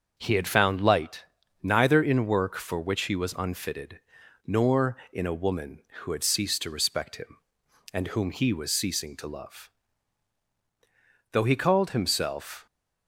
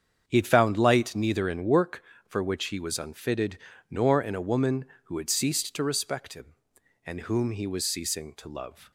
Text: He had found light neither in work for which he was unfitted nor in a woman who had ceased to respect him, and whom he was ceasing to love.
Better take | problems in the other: second | starts louder than the rest; until 1.1 s; 6 dB; strong in the second // pauses between "light" and "neither"; at 1.2 s; 0.38 s long // pauses between "unfitted" and "nor"; noticeable; at 3.9 s; 0.46 s long; slight in the second // goes on to say "Though he called himself"; from 11.3 s on; 1.3 s long

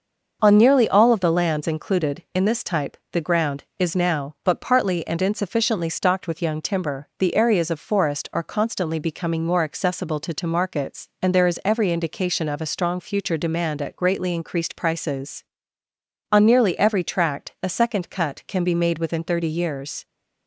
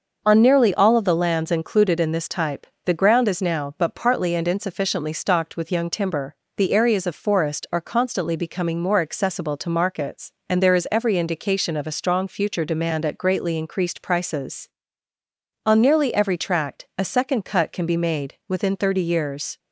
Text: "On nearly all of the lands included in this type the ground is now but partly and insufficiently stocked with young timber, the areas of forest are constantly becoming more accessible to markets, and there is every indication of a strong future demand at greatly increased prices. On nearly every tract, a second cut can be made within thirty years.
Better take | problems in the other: second | starts louder than the rest; until 1.4 s; 6 dB; also in the second // pauses between "type" and "the"; slight; at 2.9 s; 0.16 s long; slight in the second // says "to" twice; at 10.3 s

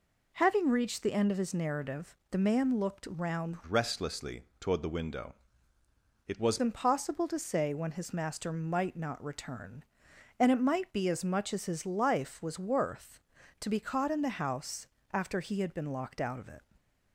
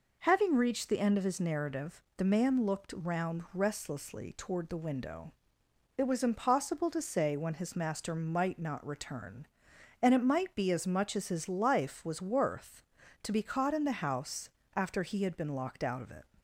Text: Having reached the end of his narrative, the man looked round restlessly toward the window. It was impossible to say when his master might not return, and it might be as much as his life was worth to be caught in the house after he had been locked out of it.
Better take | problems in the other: second | changes voice from "restlessly" to "was"; from 3.6 to 6.5 s; 2.9 s long // pauses between "restlessly" and "toward"; slight; at 4.4 s; 0.16 s long // pauses between "house" and "after"; slight; at 14.8 s; 0.28 s long; slight in the second

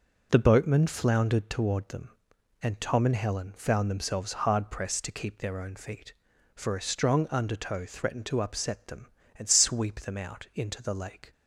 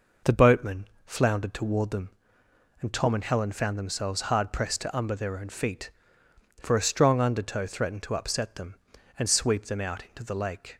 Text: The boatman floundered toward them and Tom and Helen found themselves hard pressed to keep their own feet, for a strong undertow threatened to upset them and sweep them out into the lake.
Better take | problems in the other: first | pauses between "boatman" and "floundered"; slight; at 0.8 s; 0.18 s long // says "umber" for "keep"; at 4.9 s

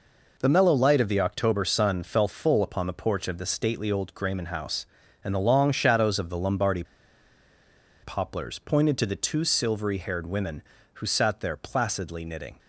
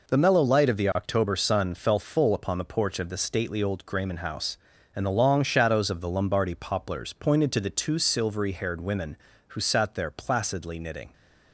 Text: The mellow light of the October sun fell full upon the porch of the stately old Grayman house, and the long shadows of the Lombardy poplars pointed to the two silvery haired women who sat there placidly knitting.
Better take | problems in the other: second | pauses between "Lombardy" and "poplars"; at 6.8 s; 1.1 s long

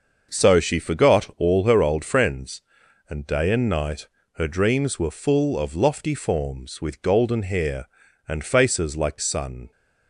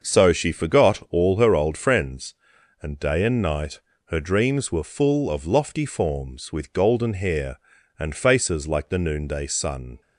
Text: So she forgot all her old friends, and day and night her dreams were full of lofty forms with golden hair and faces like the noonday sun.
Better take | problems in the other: second | starts louder than the rest; until 1.4 s; 6 dB; also in the second // pauses between "night" and "her"; slight; at 4.0 s; 0.28 s long; slight in the second // skips "the noonday"; at 9.1 s

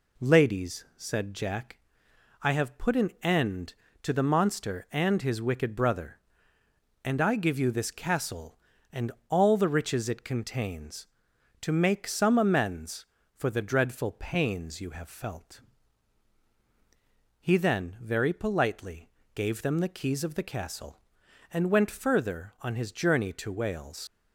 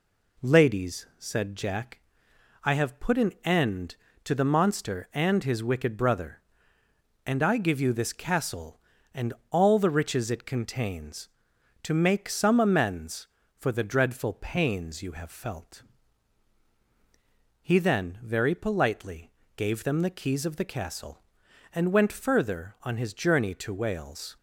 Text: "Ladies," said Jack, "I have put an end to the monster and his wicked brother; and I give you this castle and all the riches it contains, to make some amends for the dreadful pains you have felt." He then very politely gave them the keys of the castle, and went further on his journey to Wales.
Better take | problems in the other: second | pauses between "and" and "all"; slight; at 9.1 s; 0.18 s long; slight in the second // pauses between "politely" and "gave"; slight; at 19.1 s; 0.24 s long; slight in the second // leaves "Wales" unfinished; at 24.0 s; 75 ms

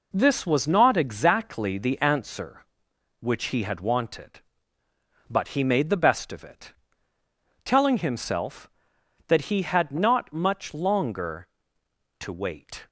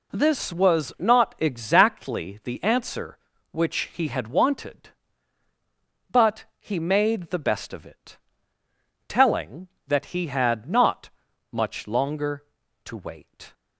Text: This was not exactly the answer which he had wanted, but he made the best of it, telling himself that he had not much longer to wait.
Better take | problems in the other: first | pauses between "but" and "he"; slight; at 6.4 s; 0.16 s long // skips "himself"; at 9.7 s // pauses between "not" and "much"; at 11.0 s; 0.44 s long

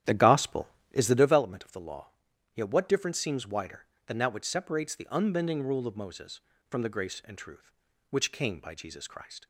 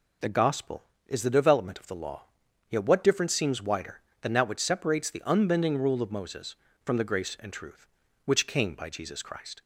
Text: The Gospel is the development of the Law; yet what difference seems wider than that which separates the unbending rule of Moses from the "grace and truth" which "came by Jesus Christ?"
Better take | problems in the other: second | starts louder than the rest; strong; until 1.5 s; 11 dB

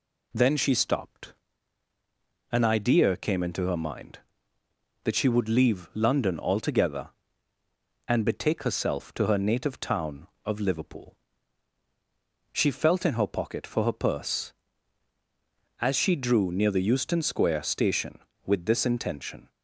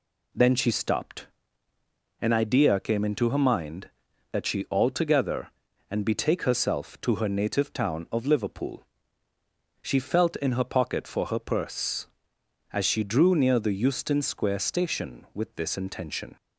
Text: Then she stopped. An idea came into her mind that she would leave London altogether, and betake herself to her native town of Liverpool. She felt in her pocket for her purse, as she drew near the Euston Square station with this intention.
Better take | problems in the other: first | skips "would leave London"; at 4.6 s

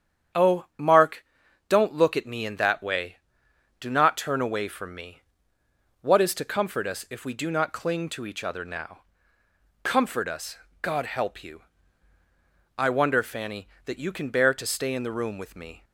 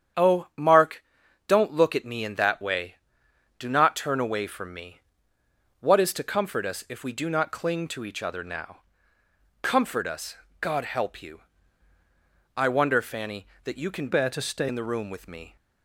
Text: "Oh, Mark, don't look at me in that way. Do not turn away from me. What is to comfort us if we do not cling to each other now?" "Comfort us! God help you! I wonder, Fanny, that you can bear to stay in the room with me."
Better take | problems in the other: first | starts louder than the rest; strong; until 1.6 s; 8.5 dB; strong in the first // changes voice from "bear" to "stay"; from 14.0 to 14.6 s; 0.6 s long

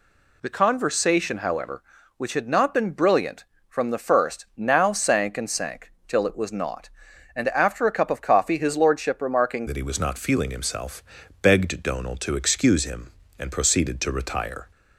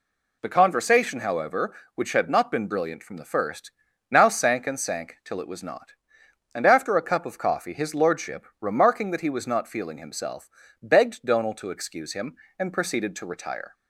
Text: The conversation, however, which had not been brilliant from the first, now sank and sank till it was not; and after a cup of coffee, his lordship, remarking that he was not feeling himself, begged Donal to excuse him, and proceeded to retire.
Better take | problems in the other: second | pauses between "sank" and "till"; slight; at 5.9 s; 0.16 s long // changes voice at "that"; from 9.6 s on; 5.1 s long

